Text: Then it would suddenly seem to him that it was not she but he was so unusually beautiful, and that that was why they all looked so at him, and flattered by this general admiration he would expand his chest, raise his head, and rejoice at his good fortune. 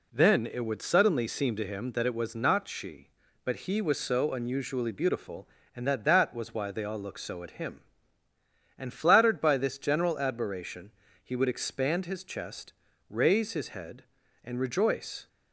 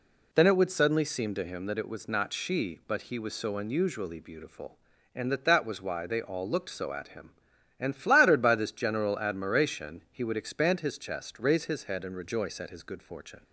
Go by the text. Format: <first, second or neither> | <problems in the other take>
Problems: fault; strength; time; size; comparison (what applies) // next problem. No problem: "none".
second | pauses between "admiration" and "he"; slight; at 10.8 s; 0.34 s long // stops before "at his good fortune"; at 15.2 s